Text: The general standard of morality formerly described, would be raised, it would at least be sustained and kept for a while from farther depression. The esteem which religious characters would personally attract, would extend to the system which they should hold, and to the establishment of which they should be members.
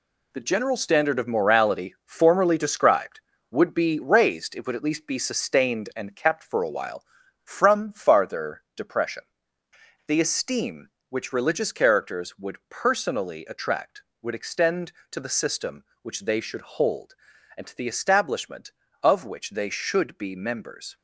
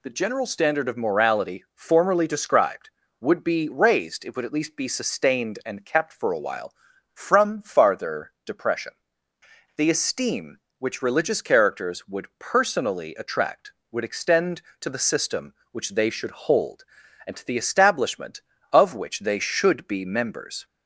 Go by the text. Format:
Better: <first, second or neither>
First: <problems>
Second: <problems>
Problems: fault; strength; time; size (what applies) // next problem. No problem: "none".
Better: second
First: gets quieter; strong; throughout; 7.5 dB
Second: none